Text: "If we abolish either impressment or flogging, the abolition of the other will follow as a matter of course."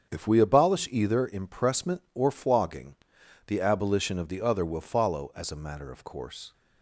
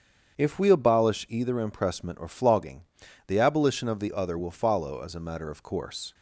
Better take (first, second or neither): neither